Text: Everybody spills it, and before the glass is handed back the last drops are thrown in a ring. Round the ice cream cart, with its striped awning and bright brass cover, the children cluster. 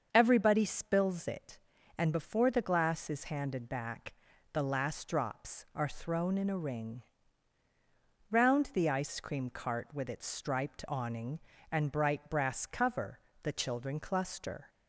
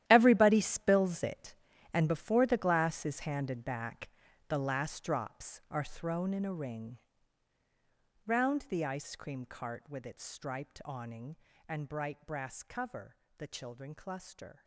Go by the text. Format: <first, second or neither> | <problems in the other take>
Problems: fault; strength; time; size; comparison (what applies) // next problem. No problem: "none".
first | gets quieter; strong; throughout; 14.5 dB // starts louder than the rest; strong; until 1.0 s; 12 dB; also in the first // pauses between "back" and "the"; at 4.0 s; 0.42 s long; also in the first